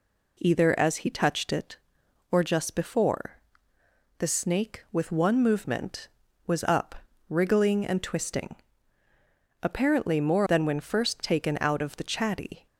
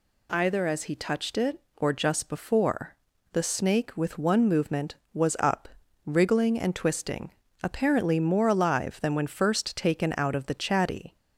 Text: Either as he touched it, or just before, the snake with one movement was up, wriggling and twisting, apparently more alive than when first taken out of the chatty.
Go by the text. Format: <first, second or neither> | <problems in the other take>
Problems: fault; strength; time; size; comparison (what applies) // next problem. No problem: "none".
second | skips "alive"; at 10.4 s